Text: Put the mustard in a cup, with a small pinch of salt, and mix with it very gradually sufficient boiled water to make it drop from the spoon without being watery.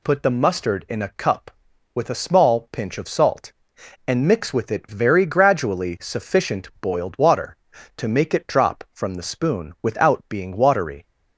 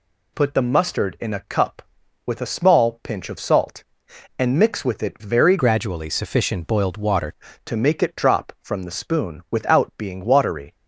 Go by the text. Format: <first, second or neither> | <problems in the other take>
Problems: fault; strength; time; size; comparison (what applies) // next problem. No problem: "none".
first | changes voice from "gradually" to "water"; from 5.5 to 7.2 s; 1.7 s long